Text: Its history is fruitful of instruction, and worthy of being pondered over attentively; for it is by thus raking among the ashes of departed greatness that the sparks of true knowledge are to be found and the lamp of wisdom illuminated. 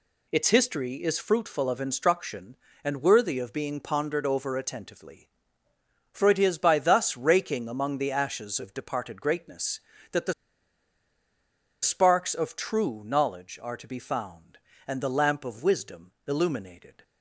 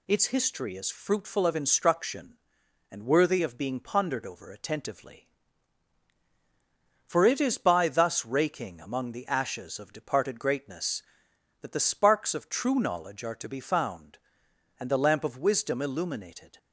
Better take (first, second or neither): second